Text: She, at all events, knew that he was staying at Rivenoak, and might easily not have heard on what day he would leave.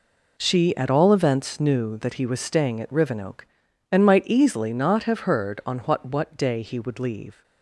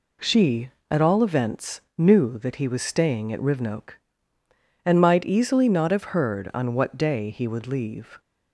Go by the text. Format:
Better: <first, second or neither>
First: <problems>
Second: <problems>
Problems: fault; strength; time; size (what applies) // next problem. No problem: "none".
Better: second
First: says "what" twice; at 6.0 s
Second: none